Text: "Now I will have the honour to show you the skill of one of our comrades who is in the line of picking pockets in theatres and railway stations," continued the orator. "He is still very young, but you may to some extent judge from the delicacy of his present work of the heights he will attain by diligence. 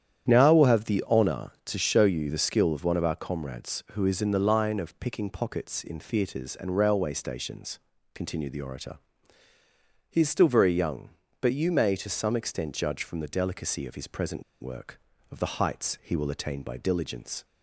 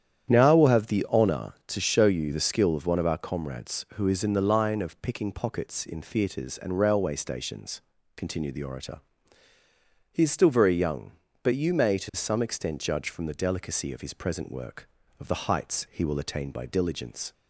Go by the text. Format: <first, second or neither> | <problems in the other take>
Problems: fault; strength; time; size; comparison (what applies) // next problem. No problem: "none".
second | starts louder than the rest; strong; until 1.3 s; 9.5 dB; strong in the second // pauses between "present" and "work"; slight; at 14.4 s; 0.19 s long